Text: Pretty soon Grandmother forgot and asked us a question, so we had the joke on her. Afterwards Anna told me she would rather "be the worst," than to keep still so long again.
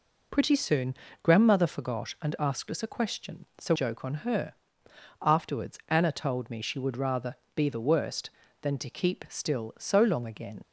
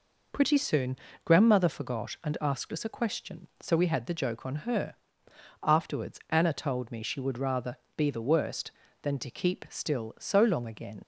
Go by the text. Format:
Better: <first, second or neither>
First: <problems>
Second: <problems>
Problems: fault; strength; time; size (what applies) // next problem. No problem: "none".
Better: second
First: pauses between "soon" and "Grandmother"; slight; at 0.9 s; 0.30 s long // skips "we had the"; at 3.7 s // pauses between "rather" and "be"; slight; at 7.3 s; 0.22 s long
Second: pauses between "soon" and "Grandmother"; slight; at 0.9 s; 0.30 s long // pauses between "rather" and "be"; slight; at 7.7 s; 0.22 s long